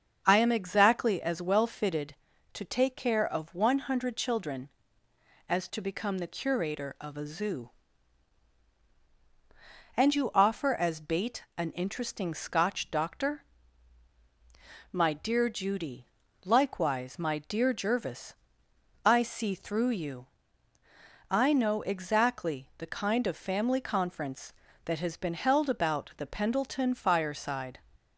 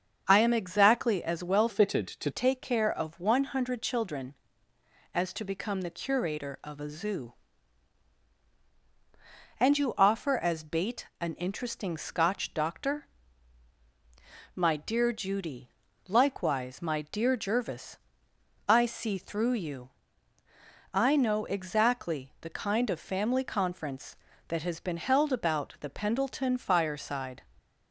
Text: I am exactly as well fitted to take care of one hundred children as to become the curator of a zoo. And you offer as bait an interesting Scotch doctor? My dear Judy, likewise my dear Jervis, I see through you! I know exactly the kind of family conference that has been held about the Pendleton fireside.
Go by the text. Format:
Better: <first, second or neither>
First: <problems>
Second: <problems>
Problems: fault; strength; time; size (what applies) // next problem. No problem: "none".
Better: first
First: starts louder than the rest; until 1.2 s; 7 dB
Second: starts louder than the rest; until 1.3 s; 7 dB // changes voice from "fitted" to "to"; from 1.6 to 2.3 s; 0.7 s long